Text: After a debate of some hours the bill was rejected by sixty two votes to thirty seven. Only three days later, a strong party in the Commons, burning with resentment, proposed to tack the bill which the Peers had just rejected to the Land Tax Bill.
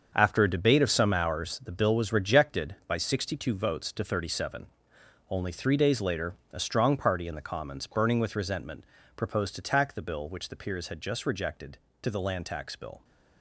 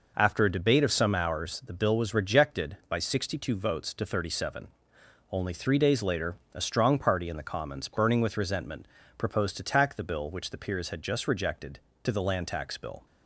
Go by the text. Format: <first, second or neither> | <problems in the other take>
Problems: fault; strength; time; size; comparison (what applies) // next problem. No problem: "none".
second | gets quieter; strong; throughout; 10.5 dB